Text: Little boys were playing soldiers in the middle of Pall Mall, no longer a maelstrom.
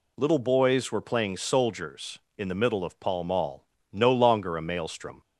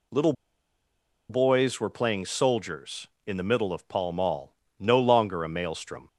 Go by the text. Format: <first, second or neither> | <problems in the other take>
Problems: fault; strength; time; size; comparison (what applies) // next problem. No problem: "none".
first | pauses between "Little" and "boys"; noticeable; at 0.3 s; 0.96 s long